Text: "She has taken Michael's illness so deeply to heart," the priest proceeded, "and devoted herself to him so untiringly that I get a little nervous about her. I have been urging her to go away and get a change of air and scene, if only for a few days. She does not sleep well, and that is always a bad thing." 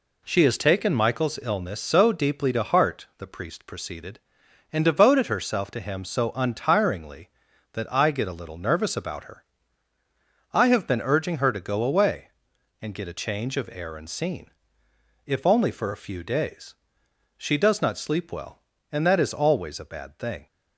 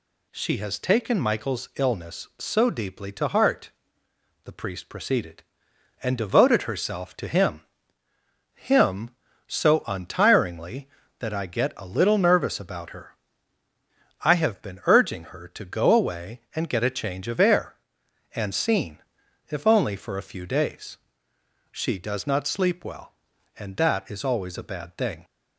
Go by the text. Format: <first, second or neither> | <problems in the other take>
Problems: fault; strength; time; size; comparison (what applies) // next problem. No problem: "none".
first | says "him" twice; at 8.5 s